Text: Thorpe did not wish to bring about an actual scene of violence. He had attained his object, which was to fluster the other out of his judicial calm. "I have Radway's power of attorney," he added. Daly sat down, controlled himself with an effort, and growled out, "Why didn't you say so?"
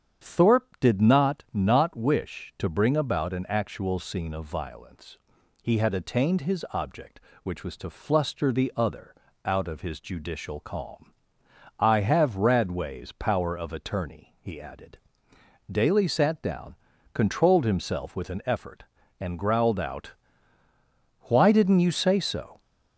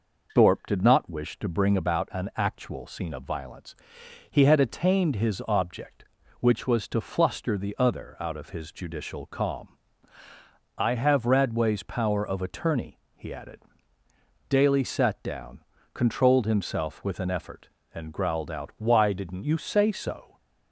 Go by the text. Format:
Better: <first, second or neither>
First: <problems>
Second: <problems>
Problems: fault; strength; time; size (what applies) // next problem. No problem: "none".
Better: second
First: starts louder than the rest; strong; until 1.2 s; 8 dB // says "not" twice; at 1.5 s // pauses between "other" and "out"; slight; at 9.1 s; 0.28 s long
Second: none